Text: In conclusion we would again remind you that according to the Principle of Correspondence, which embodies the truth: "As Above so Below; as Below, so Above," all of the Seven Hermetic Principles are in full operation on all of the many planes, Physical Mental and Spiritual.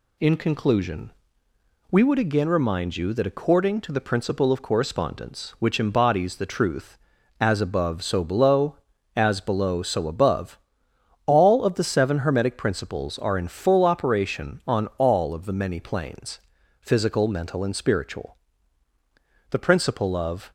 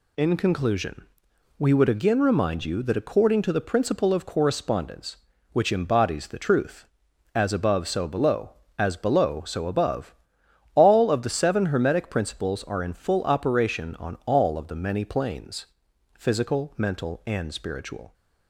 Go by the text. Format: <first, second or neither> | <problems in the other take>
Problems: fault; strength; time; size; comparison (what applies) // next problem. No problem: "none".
second | pauses between "conclusion" and "we"; noticeable; at 1.1 s; 0.80 s long; noticeable in the second // goes on to say "The Principle of"; noticeable; from 19.5 s on; 1.0 s long